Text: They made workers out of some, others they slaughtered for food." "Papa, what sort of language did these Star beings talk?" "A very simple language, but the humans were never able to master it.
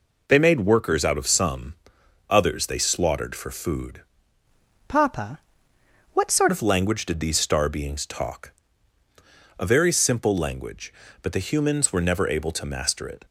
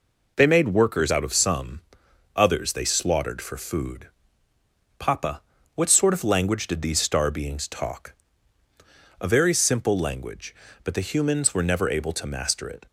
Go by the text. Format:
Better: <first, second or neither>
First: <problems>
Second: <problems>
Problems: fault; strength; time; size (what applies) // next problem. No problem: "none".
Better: second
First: changes voice from "Papa" to "sort"; from 4.8 to 6.4 s; 1.6 s long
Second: none